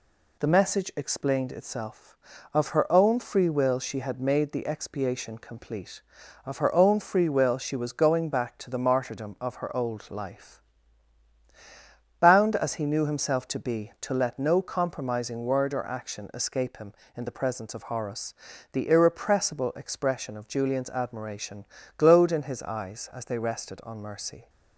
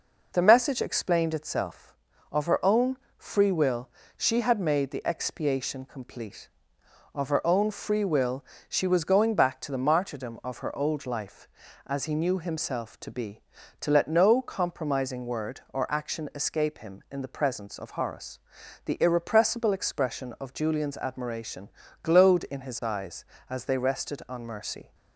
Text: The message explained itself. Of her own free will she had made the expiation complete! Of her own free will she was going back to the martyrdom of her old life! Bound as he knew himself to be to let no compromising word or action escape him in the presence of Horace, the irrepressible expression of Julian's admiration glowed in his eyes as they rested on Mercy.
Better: first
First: pauses between "admiration" and "glowed"; slight; at 21.6 s; 0.32 s long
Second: pauses between "own" and "free"; slight; at 2.9 s; 0.22 s long // pauses between "will" and "she"; slight; at 3.8 s; 0.26 s long // pauses between "will" and "she"; slight; at 8.4 s; 0.28 s long // skips "Bound"; at 11.6 s // pauses between "admiration" and "glowed"; slight; at 21.6 s; 0.36 s long

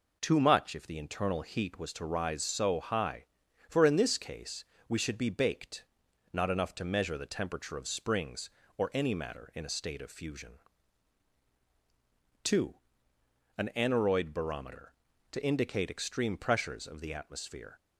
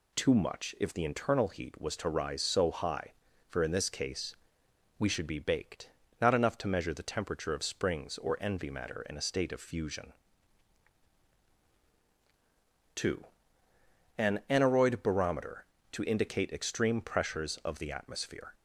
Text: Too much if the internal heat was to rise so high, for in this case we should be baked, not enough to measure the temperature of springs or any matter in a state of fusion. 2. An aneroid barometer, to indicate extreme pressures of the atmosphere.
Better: first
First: pauses between "case" and "we"; slight; at 4.6 s; 0.24 s long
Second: pauses between "case" and "we"; noticeable; at 4.3 s; 0.63 s long // says "envy" for "any"; at 8.3 s

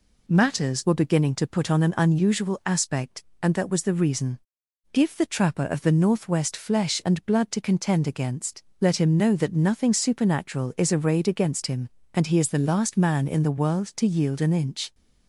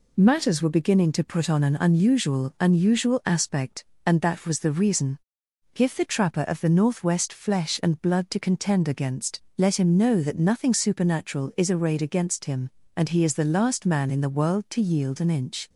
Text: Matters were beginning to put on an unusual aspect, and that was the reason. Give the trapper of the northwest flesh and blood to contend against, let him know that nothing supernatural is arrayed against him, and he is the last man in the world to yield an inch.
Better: first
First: none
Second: says "unusual" twice; at 2.5 s

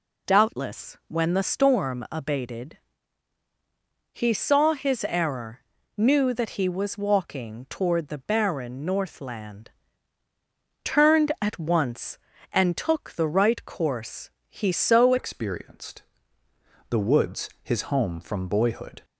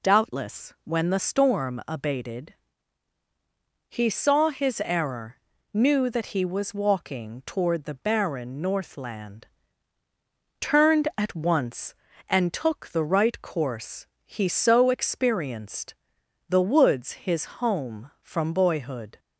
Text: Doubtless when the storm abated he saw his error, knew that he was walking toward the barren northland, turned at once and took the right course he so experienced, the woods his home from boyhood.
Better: second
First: pauses between "abated" and "he"; strong; at 2.7 s; 1.4 s long // pauses between "course" and "he"; slight; at 14.2 s; 0.20 s long // changes voice at "experienced"; from 15.1 s on; 3.9 s long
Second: pauses between "abated" and "he"; strong; at 2.5 s; 1.4 s long // pauses between "course" and "he"; slight; at 14.0 s; 0.20 s long

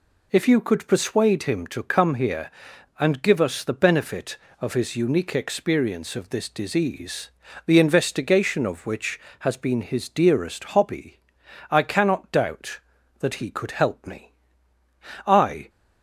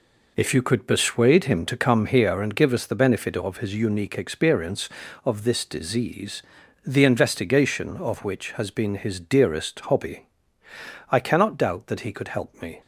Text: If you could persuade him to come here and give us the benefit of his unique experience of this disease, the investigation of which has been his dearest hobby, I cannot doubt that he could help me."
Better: second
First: goes on to say "I"; slight; from 15.2 s on; 0.44 s long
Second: none

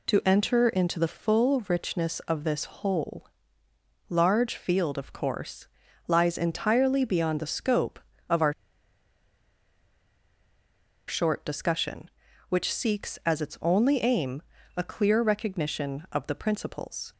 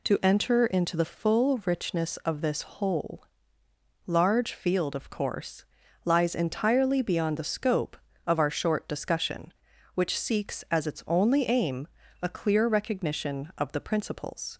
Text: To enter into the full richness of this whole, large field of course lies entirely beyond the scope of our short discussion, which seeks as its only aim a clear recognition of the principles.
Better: second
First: pauses between "course" and "lies"; at 5.6 s; 0.40 s long // pauses between "our" and "short"; strong; at 8.5 s; 2.5 s long // pauses between "aim" and "a"; slight; at 14.4 s; 0.34 s long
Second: pauses between "course" and "lies"; at 5.6 s; 0.40 s long // pauses between "aim" and "a"; slight; at 11.8 s; 0.34 s long

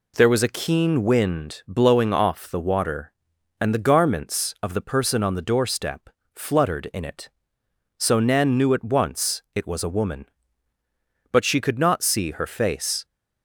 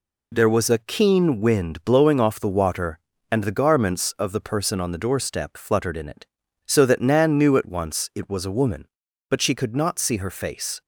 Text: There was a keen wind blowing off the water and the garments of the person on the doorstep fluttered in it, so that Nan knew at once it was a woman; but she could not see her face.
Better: second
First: pauses between "doorstep" and "fluttered"; slight; at 6.0 s; 0.24 s long // skips "that"; at 8.2 s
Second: none

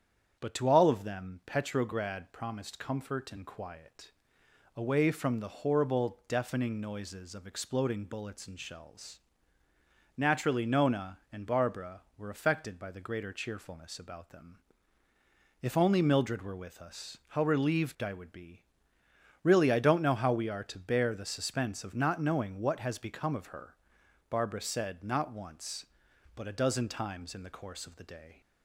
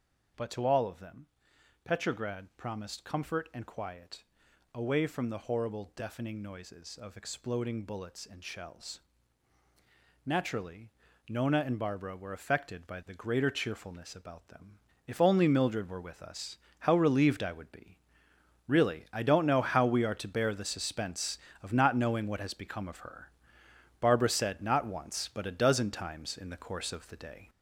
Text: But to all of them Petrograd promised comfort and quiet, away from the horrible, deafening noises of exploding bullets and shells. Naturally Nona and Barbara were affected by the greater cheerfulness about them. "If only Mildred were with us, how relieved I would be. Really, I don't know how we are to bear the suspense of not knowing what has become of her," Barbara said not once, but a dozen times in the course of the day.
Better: first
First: starts louder than the rest; strong; until 1.4 s; 8 dB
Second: gets louder; noticeable; throughout; 6 dB // starts louder than the rest; until 1.9 s; 7 dB // pauses between "them" and "Petrograd"; noticeable; at 1.2 s; 0.58 s long // pauses between "Naturally" and "Nona"; at 10.9 s; 0.38 s long

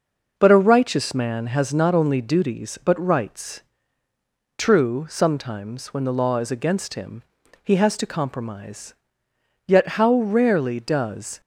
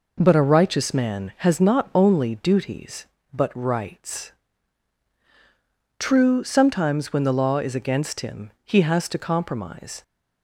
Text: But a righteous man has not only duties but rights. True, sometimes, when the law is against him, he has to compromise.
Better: second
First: goes on to say "Yet how rarely does"; strong; from 9.6 s on; 1.7 s long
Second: none

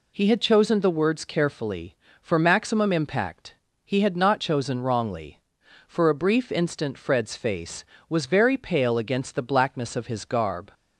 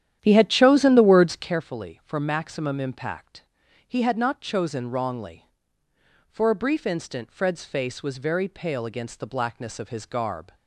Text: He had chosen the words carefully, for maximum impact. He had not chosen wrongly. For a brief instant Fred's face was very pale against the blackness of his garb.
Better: first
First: none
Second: starts louder than the rest; strong; until 1.5 s; 10.5 dB

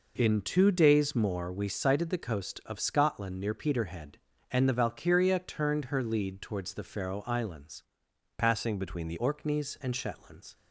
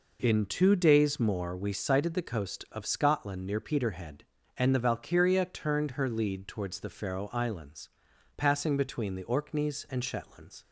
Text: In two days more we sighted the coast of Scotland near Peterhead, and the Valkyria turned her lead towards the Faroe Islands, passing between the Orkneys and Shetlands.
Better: second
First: changes voice from "passing" to "the"; from 8.3 to 9.1 s; 0.8 s long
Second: none

